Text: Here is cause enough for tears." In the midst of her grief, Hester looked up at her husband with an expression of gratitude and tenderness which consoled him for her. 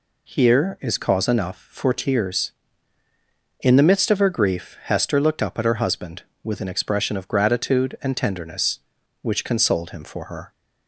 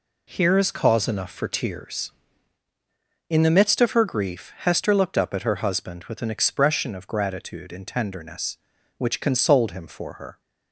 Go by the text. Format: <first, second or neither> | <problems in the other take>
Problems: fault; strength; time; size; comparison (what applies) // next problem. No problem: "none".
neither | none